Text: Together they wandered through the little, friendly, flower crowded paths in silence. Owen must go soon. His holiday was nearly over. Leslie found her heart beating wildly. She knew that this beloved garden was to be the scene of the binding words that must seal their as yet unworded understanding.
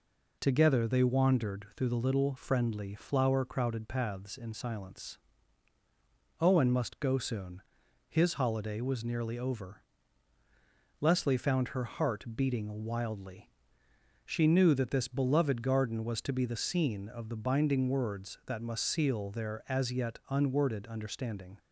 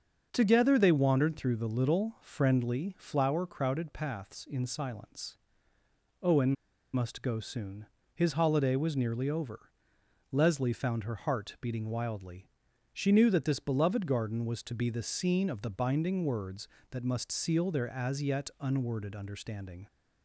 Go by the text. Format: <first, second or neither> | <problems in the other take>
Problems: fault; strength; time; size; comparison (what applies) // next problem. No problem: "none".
first | starts louder than the rest; until 1.3 s; 6.5 dB // pauses between "Owen" and "must"; at 6.5 s; 0.39 s long